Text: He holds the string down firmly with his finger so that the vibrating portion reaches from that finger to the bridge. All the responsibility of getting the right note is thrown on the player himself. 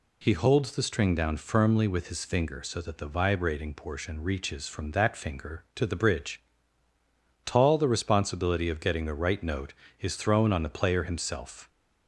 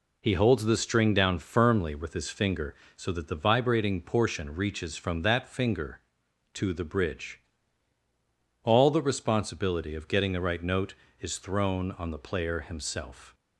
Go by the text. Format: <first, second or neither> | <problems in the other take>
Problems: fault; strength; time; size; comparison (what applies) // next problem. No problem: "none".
second | says "Tall" for "All"; at 7.4 s